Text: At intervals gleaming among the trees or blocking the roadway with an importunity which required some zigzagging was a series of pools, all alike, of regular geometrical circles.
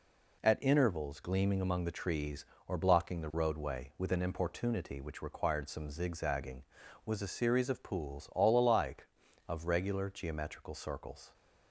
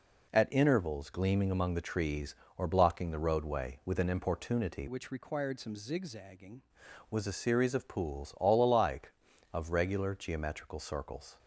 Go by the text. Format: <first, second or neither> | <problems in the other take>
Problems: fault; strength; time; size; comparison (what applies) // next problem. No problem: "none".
first | changes voice from "which" to "zigzagging"; from 4.8 to 6.6 s; 1.8 s long